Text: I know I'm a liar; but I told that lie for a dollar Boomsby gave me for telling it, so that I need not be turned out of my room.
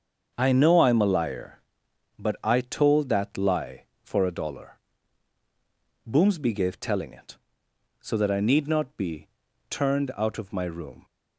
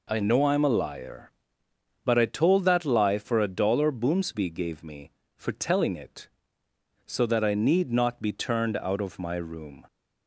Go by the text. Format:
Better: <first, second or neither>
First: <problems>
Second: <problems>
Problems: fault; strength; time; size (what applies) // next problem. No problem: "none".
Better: second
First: starts louder than the rest; until 1.3 s; 6.5 dB // pauses between "dollar" and "Boomsby"; strong; at 4.7 s; 1.3 s long // skips "me for"; at 6.7 s // pauses between "be" and "turned"; at 9.2 s; 0.42 s long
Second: none